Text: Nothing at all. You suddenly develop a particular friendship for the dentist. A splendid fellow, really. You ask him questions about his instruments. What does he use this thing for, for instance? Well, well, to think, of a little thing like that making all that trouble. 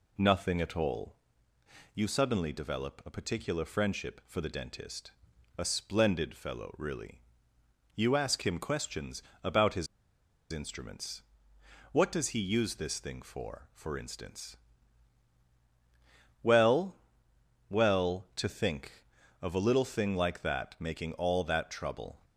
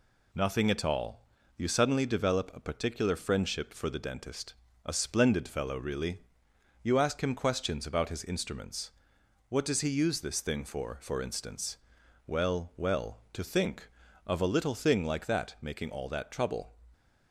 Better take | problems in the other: second | pauses between "questions" and "about"; slight; at 9.2 s; 0.22 s long // pauses between "his" and "instruments"; noticeable; at 9.8 s; 0.64 s long

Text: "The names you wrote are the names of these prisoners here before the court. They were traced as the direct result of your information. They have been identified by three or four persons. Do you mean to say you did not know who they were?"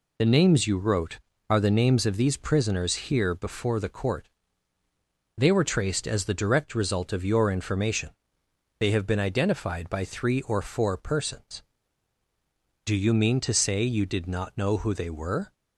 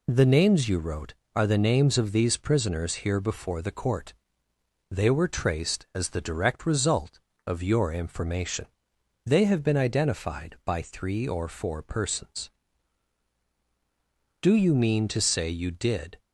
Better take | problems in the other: first | stops before "not know who they were"; at 16.1 s

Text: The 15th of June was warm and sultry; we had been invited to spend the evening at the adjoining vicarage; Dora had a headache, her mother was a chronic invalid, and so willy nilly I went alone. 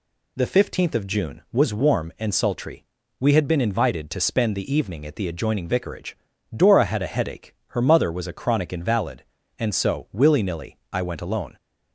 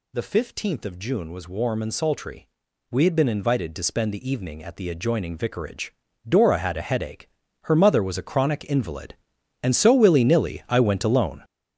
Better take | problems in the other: first | gets louder; strong; throughout; 8.5 dB

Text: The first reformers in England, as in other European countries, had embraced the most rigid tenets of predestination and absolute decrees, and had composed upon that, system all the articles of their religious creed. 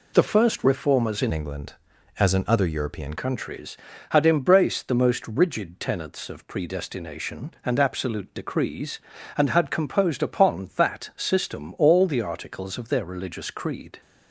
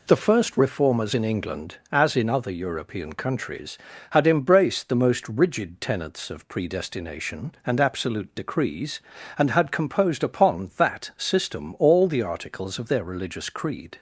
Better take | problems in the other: second | changes voice from "England" to "European"; from 1.3 to 3.1 s; 1.8 s long

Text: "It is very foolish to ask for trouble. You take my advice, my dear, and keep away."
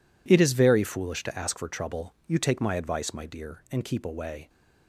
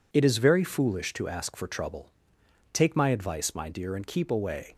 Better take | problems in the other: first | skips "You"; at 2.4 s

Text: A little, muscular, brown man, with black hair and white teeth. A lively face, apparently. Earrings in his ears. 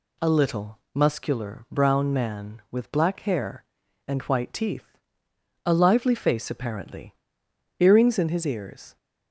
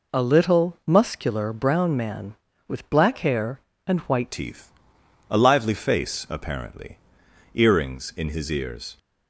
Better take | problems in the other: first | changes voice at "teeth"; from 4.3 s on; 4.6 s long

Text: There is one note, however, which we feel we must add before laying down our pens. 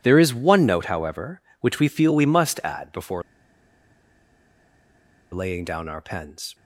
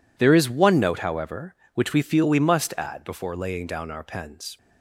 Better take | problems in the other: second | pauses between "before" and "laying"; strong; at 3.2 s; 2.1 s long

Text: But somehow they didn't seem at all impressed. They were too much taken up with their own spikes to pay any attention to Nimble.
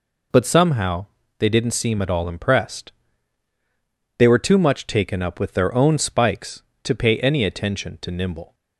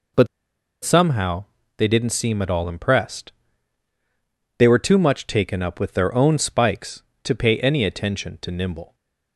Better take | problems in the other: first | pauses between "But" and "somehow"; noticeable; at 0.2 s; 0.57 s long // pauses between "somehow" and "they"; slight; at 1.4 s; 0.34 s long; slight in the first // stays silent after the last word; slight; from 8.8 s on; 0.5 s long

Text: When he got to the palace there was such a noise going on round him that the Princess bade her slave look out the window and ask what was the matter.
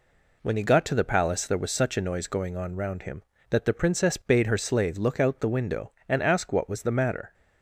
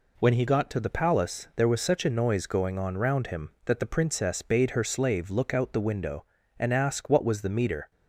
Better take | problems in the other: first | says "meter" for "matter"; at 7.5 s

